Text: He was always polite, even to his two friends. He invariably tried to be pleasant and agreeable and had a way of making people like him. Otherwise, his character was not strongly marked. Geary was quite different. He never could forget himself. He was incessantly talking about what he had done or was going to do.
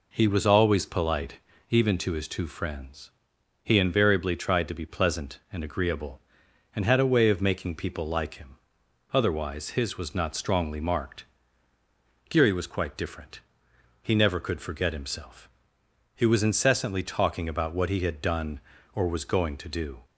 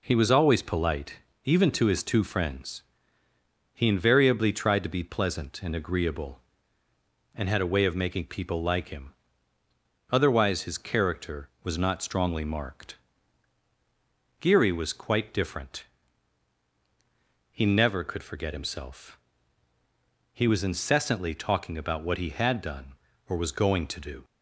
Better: second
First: skips "character"; at 9.9 s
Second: none

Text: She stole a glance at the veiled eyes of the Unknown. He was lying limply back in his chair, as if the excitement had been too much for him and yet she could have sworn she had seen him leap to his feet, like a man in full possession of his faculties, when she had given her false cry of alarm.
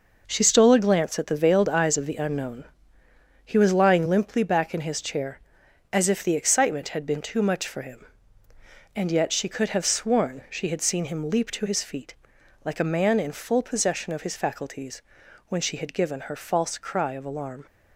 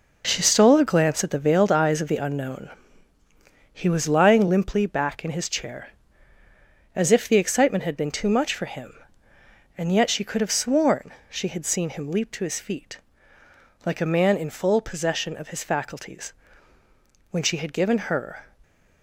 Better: first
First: none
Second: pauses between "sworn" and "she"; slight; at 11.1 s; 0.18 s long // stops before "false cry of alarm"; at 18.6 s

